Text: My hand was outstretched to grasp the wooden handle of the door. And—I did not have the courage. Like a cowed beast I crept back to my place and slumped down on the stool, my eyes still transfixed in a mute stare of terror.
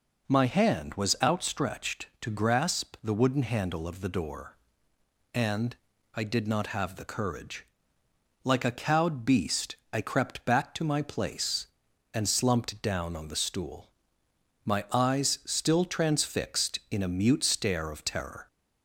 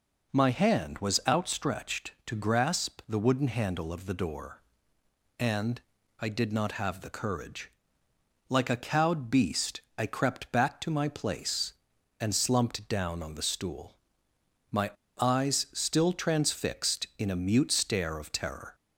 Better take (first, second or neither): first